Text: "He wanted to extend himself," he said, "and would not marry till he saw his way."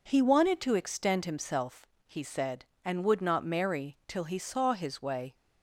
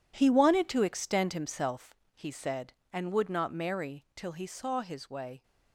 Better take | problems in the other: first | gets quieter; strong; throughout; 13 dB

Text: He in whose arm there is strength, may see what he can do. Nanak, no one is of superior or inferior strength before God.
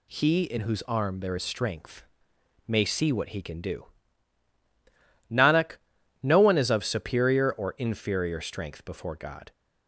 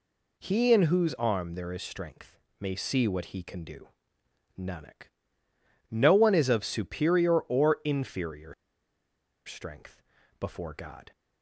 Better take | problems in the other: first | pauses between "inferior" and "strength"; noticeable; at 8.5 s; 0.92 s long // pauses between "strength" and "before"; at 10.0 s; 0.38 s long

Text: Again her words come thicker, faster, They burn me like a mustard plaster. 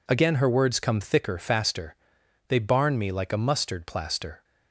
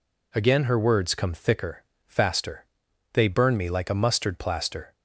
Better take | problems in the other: second | says "barn" for "burn"; at 2.5 s

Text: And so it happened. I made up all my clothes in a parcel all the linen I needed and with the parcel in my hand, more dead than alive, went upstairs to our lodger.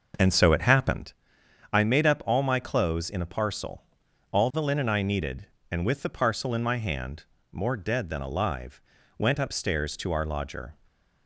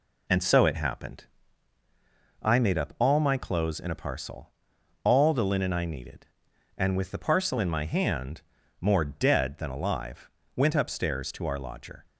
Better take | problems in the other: second | starts louder than the rest; noticeable; until 1.0 s; 6 dB // pauses between "parcel" and "all"; noticeable; at 3.8 s; 0.50 s long; noticeable in the second // stays silent after the last word; slight; from 10.7 s on; 0.5 s long

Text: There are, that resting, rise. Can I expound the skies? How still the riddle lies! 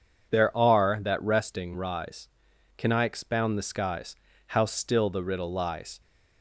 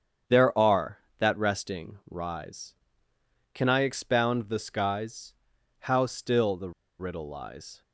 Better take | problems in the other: first | starts louder than the rest; strong; until 1.5 s; 8 dB // pauses between "the" and "riddle"; slight; at 6.7 s; 0.28 s long

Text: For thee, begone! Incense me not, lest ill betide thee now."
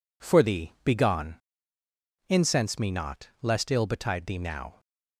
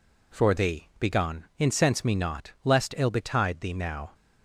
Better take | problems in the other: neither | none

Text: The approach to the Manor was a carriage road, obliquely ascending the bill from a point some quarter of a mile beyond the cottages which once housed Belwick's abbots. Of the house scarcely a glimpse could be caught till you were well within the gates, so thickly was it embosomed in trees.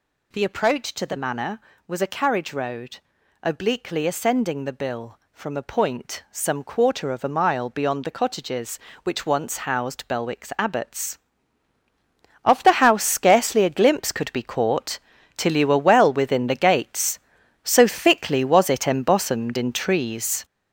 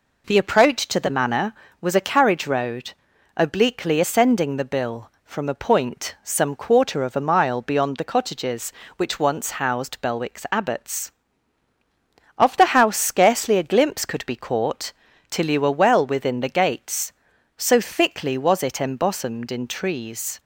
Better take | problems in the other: second | gets louder; strong; throughout; 8 dB // pauses between "caught" and "till"; at 14.9 s; 0.38 s long; also in the second

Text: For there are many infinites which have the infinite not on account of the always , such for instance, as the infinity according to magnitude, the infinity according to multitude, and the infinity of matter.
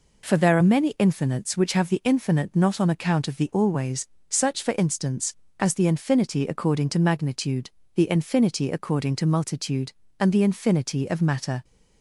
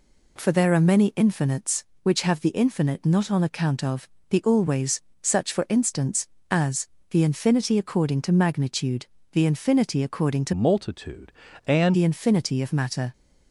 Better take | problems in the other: first | pauses between "of" and "the"; slight; at 4.0 s; 0.22 s long // pauses between "as" and "the"; slight; at 6.8 s; 0.24 s long // changes voice from "multitude" to "and"; from 10.5 to 11.9 s; 1.4 s long

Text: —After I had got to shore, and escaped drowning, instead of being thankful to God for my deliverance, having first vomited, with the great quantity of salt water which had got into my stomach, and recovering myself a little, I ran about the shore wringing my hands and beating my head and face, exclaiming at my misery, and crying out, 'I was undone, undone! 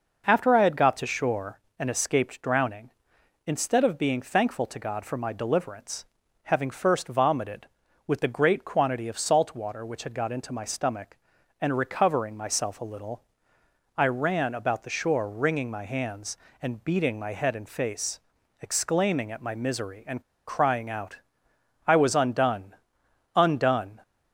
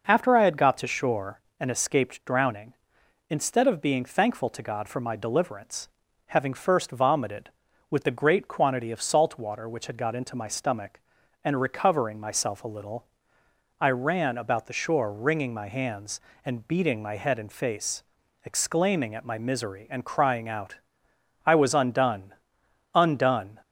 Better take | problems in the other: second | pauses between "and" and "crying"; slight; at 20.2 s; 0.24 s long

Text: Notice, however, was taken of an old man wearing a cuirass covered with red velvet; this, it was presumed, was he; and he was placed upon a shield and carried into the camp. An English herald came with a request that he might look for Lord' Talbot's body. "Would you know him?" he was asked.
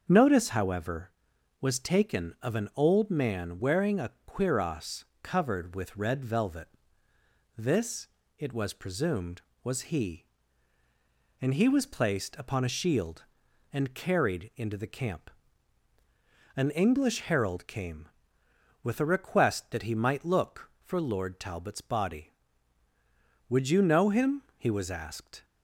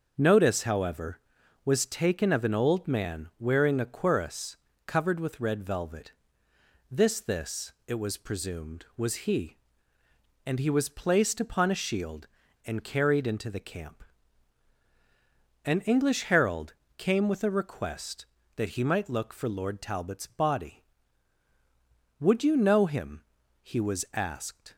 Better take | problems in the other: first | starts louder than the rest; until 1.1 s; 6.5 dB; also in the first // pauses between "cuirass" and "covered"; slight; at 4.5 s; 0.30 s long; slight in the first // says "this" twice; at 7.2 s // pauses between "herald" and "came"; slight; at 16.7 s; 0.24 s long

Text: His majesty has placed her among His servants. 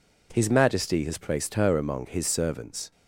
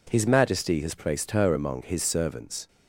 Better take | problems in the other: neither | none

